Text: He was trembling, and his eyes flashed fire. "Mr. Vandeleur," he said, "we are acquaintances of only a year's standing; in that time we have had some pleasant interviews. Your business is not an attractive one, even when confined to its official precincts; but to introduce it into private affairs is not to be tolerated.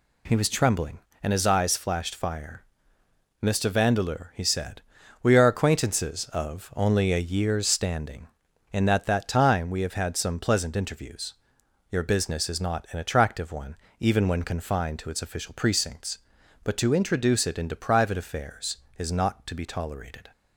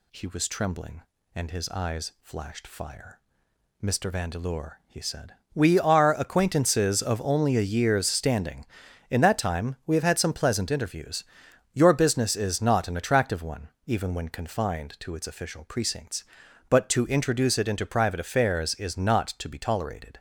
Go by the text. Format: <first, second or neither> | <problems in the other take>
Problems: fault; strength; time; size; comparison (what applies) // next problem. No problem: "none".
second | says "that" twice; at 9.0 s